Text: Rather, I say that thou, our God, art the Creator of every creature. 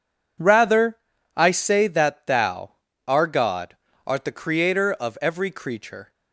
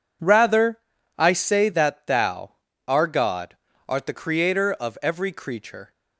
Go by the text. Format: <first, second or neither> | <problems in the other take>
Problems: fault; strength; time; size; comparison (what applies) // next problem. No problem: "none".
neither | none